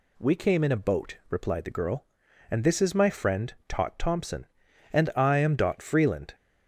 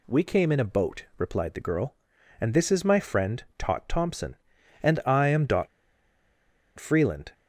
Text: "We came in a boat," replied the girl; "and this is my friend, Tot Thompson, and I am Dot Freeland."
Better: first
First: none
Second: pauses between "Dot" and "Freeland"; at 5.6 s; 1.1 s long

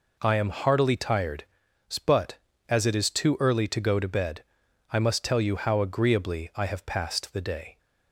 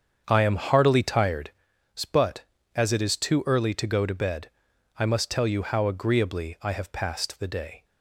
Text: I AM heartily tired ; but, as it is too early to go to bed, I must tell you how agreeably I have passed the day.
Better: first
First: none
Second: starts louder than the rest; strong; until 1.4 s; 7.5 dB

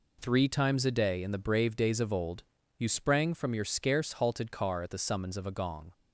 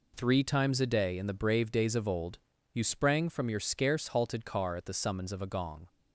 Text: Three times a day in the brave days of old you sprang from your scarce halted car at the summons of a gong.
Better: neither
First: pauses between "old" and "you"; slight; at 2.4 s; 0.34 s long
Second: pauses between "old" and "you"; slight; at 2.3 s; 0.34 s long

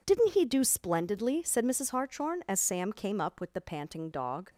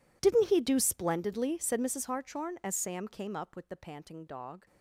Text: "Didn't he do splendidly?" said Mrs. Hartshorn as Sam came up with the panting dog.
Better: first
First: none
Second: gets quieter; strong; throughout; 21.5 dB

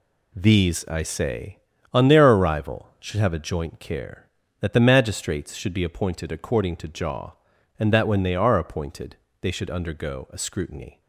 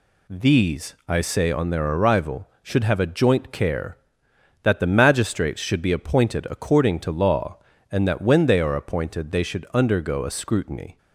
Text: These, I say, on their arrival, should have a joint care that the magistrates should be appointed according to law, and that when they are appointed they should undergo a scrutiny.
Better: second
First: says "jaw" for "law"; at 6.8 s // pauses between "appointed" and "they"; slight; at 9.1 s; 0.24 s long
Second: none

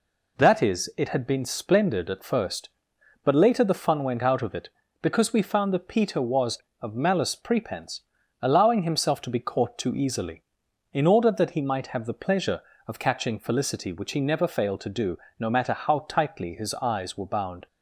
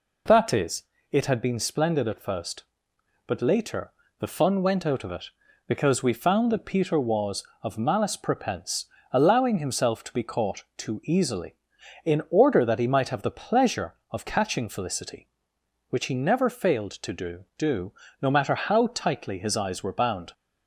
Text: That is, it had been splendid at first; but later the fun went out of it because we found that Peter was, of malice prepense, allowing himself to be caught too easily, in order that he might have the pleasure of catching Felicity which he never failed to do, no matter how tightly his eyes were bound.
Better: first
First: none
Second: pauses between "later" and "the"; slight; at 3.9 s; 0.26 s long // says "do" twice; at 17.5 s

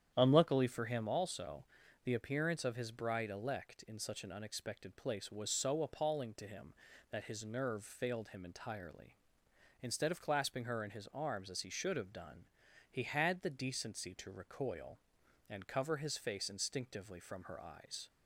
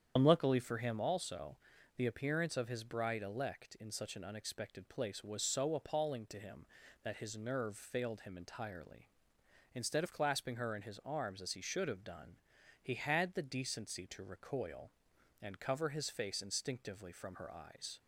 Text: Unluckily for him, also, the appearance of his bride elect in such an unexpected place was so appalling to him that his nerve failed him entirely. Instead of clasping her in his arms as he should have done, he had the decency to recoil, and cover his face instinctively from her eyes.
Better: first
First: starts louder than the rest; strong; until 1.1 s; 9.5 dB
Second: loses the start of "Unluckily"; at 0.1 s; 80 ms // starts louder than the rest; strong; until 1.1 s; 8.5 dB

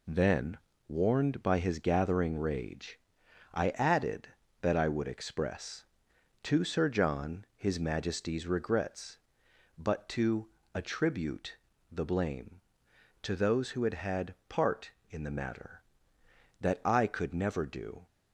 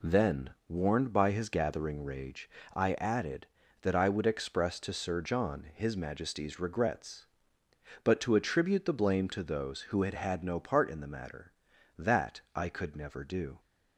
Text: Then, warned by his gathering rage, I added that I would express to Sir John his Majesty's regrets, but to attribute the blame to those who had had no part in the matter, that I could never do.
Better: second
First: pauses between "to" and "attribute"; slight; at 10.4 s; 0.26 s long // pauses between "attribute" and "the"; slight; at 11.5 s; 0.34 s long // skips "no"; at 14.4 s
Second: none

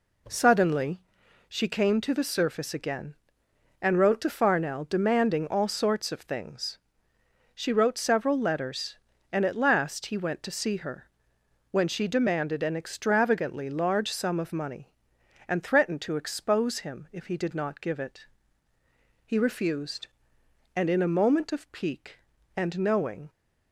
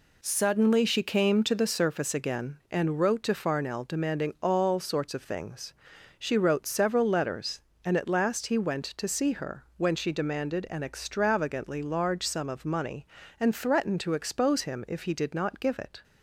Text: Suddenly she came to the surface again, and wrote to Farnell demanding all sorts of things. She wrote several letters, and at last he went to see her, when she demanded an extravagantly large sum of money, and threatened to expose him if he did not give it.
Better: second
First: pauses between "Suddenly" and "she"; noticeable; at 1.0 s; 0.46 s long // goes on to say "He refused and in a moment of pique and knowing"; strong; from 19.2 s on; 4.0 s long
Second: none

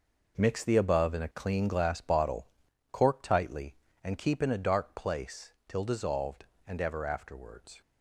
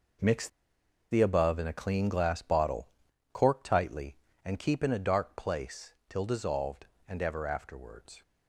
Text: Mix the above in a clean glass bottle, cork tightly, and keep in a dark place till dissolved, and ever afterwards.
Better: first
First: pauses between "place" and "till"; slight; at 5.5 s; 0.16 s long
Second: pauses between "Mix" and "the"; noticeable; at 0.4 s; 0.62 s long // pauses between "place" and "till"; slight; at 5.9 s; 0.16 s long

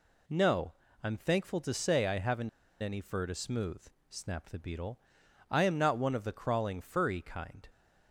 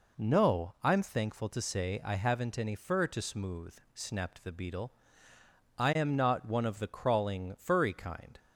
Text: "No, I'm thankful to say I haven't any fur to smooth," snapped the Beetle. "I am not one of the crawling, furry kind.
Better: second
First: pauses between "haven't" and "any"; slight; at 2.4 s; 0.31 s long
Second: none

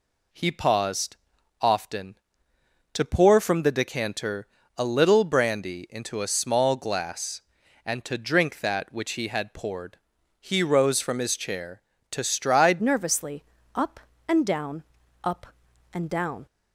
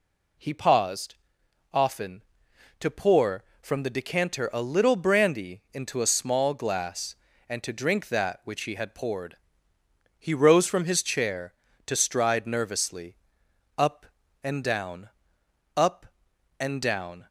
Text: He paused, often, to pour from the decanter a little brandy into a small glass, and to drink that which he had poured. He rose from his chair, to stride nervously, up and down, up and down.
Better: second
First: pauses between "decanter" and "a"; slight; at 4.4 s; 0.30 s long // changes voice at "nervously"; from 12.8 s on; 3.6 s long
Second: none

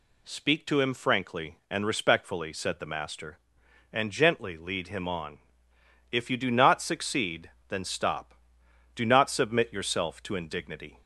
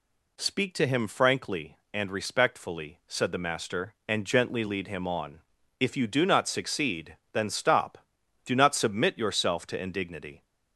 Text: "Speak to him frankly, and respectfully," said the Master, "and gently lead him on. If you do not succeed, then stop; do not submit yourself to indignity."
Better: neither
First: none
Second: none

